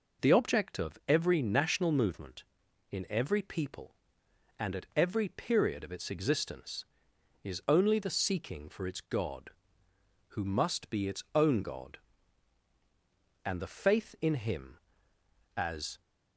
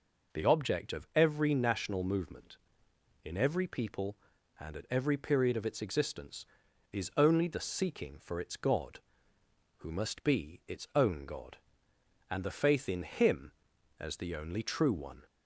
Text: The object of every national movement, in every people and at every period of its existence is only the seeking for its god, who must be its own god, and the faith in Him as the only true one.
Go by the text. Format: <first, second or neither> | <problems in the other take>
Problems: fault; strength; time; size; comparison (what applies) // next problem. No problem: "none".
second | stops before "the only true one"; at 16.0 s